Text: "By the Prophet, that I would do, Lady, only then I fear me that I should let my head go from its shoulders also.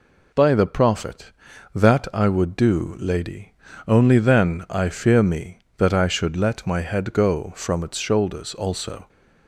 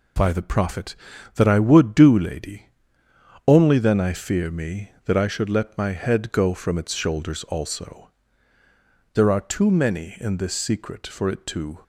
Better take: first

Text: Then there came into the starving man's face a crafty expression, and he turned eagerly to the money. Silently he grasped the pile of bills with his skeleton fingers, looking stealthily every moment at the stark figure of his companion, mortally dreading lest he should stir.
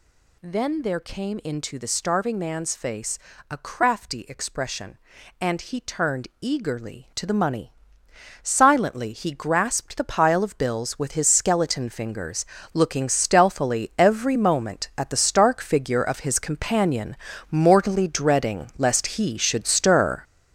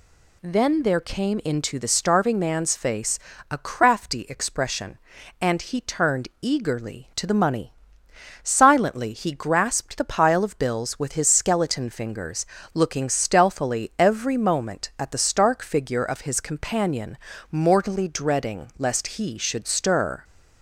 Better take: second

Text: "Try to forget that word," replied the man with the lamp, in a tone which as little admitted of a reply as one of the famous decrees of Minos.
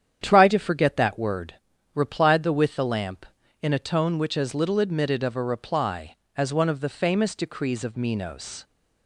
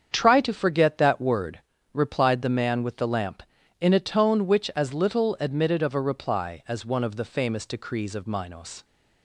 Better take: second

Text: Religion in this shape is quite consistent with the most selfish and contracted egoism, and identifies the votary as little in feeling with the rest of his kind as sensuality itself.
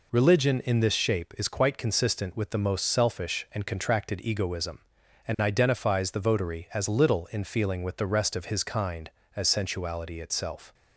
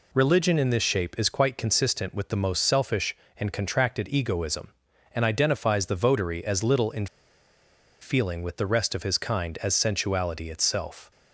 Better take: first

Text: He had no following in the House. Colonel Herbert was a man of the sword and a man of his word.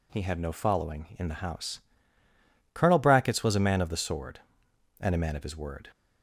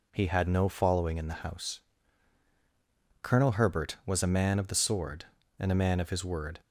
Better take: second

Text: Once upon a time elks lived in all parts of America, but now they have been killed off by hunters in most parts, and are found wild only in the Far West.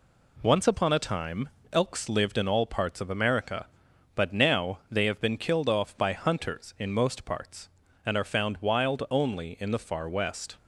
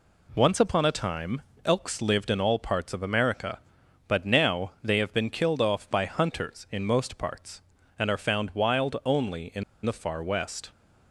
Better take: first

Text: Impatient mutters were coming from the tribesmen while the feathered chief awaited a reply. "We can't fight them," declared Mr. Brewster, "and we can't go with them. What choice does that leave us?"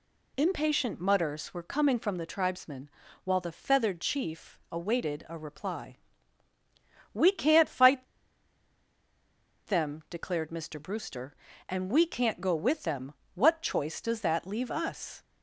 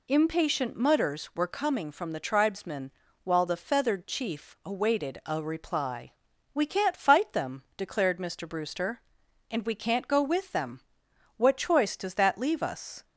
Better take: second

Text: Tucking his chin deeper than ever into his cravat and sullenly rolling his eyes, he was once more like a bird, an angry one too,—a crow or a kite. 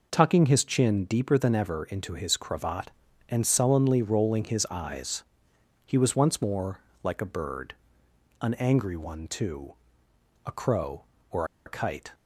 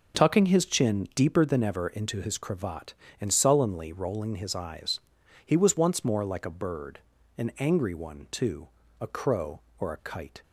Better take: second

